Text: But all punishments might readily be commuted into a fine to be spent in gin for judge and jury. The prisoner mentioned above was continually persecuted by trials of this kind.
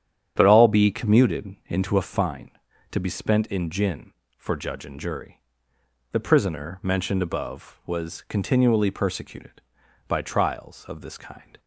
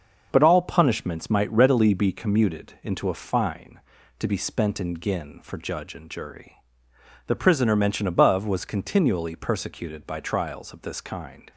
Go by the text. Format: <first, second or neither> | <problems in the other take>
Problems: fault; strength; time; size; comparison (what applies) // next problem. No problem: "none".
second | starts louder than the rest; strong; until 1.3 s; 9 dB; also in the second // skips "punishments might readily"; at 0.6 s